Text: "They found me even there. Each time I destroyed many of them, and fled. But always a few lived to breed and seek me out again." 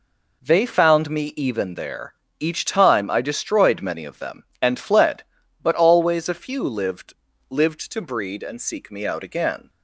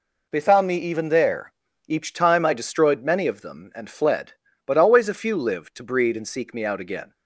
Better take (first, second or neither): second